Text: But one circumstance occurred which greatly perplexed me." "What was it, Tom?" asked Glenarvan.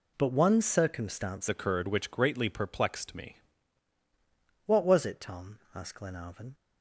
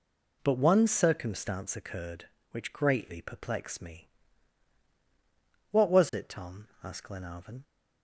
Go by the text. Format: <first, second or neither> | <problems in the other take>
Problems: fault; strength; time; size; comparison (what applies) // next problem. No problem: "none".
second | changes voice from "occurred" to "me"; from 1.4 to 3.3 s; 1.9 s long